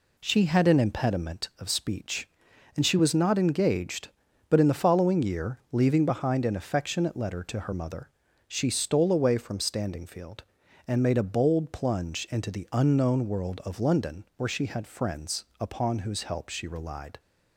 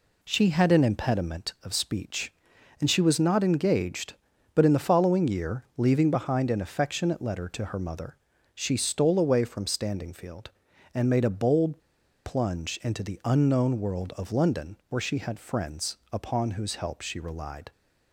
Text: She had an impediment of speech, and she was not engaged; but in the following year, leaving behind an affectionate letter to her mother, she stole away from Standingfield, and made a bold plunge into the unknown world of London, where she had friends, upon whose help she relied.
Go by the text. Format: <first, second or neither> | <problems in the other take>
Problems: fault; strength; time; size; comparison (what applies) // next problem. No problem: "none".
first | pauses between "bold" and "plunge"; noticeable; at 11.7 s; 0.46 s long